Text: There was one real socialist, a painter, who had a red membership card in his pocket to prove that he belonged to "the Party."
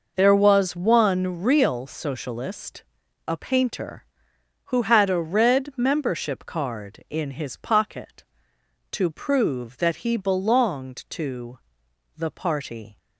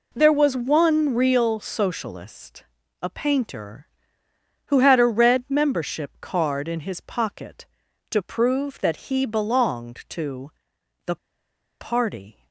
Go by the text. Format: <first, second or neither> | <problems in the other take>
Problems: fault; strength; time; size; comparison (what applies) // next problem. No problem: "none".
first | pauses between "to" and "the"; noticeable; at 10.5 s; 0.54 s long; noticeable in the first // pauses between "the" and "Party"; noticeable; at 11.1 s; 0.64 s long